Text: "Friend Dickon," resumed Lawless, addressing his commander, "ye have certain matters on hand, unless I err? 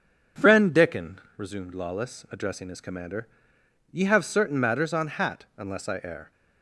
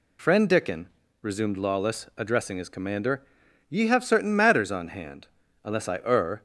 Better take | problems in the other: second | says "hat" for "hand"; at 5.0 s

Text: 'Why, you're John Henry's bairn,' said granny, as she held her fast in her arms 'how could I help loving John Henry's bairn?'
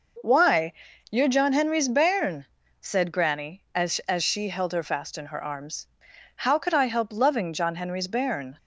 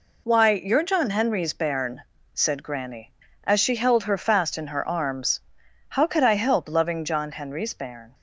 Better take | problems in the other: second | says "as" twice; at 4.0 s // pauses between "arms" and "how"; noticeable; at 5.8 s; 0.50 s long; noticeable in the second

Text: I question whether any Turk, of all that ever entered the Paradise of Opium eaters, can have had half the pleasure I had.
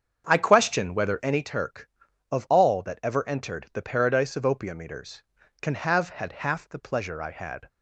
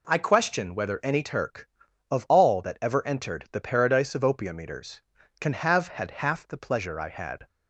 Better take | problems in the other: second | starts louder than the rest; strong; until 1.4 s; 7 dB

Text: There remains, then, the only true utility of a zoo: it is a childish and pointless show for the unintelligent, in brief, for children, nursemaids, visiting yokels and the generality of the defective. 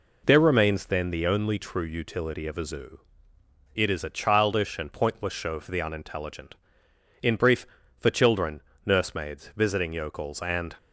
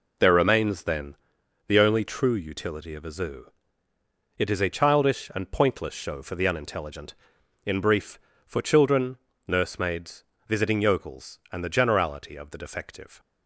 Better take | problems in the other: second | stops before "the generality of the defective"; at 10.7 s

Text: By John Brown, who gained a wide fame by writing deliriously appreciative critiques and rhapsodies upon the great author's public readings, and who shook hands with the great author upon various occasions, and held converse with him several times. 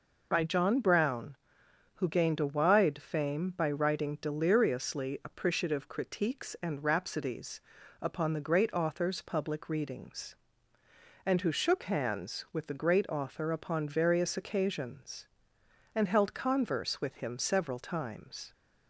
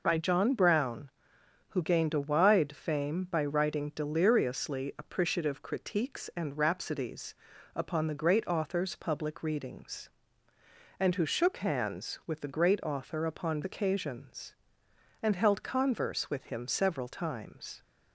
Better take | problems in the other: first | pauses between "rhapsodies" and "upon"; at 7.3 s; 0.40 s long; also in the first // skips "various"; at 13.6 s

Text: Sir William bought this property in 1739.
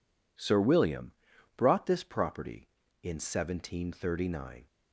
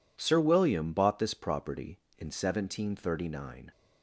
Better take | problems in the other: second | says "brought" for "bought"; at 1.5 s

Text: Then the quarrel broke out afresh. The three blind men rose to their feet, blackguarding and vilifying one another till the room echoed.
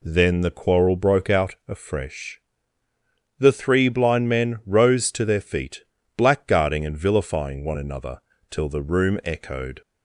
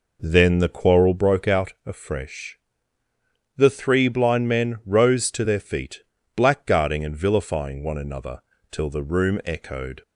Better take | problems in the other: first | starts louder than the rest; noticeable; until 1.3 s; 4.5 dB // pauses between "another" and "till"; slight; at 8.4 s; 0.28 s long; slight in the first

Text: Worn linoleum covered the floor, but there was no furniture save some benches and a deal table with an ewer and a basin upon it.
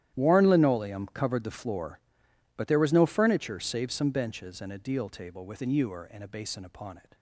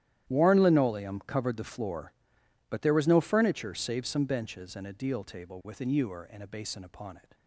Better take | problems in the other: neither | starts louder than the rest; strong; the same in both

